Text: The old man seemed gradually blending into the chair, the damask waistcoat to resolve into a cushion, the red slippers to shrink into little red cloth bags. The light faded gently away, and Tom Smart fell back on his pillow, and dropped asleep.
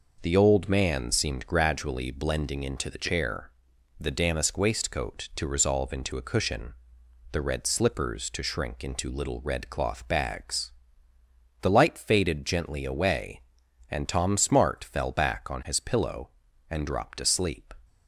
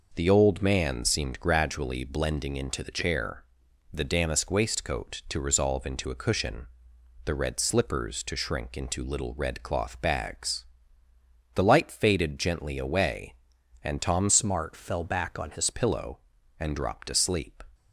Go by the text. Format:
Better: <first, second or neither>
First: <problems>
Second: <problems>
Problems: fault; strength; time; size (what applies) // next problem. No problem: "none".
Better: first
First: none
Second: changes voice from "Smart" to "his"; from 14.2 to 15.7 s; 1.5 s long